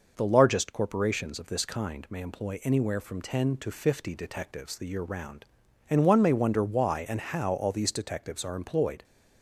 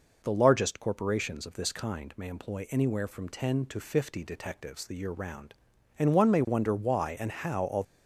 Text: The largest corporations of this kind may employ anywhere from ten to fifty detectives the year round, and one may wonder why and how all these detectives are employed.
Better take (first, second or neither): first